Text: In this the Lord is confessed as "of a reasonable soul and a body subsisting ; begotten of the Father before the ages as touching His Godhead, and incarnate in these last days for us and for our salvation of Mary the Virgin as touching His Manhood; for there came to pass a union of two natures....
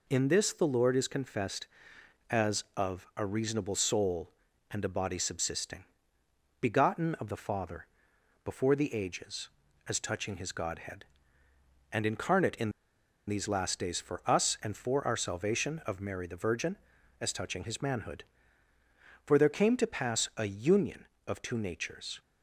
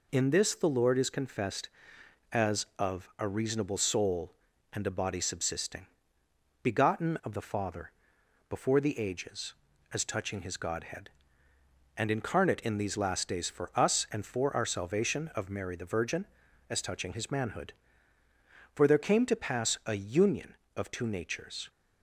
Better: second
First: pauses between "Father" and "before"; noticeable; at 7.8 s; 0.56 s long // pauses between "in" and "these"; noticeable; at 12.7 s; 0.57 s long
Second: pauses between "Father" and "before"; noticeable; at 7.9 s; 0.56 s long

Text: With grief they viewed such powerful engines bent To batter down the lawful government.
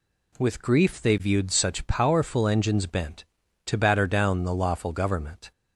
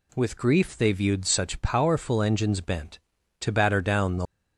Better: first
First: none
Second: stops before "lawful government"; at 4.2 s

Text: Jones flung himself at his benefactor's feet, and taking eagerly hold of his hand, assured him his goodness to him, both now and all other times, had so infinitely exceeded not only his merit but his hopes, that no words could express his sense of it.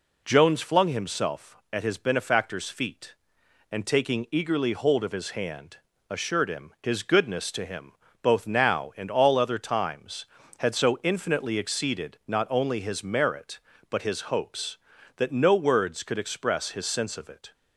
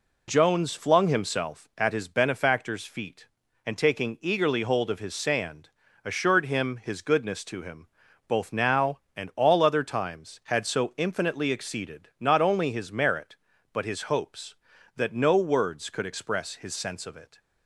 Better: first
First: none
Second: says "sand" for "hand"; at 5.1 s

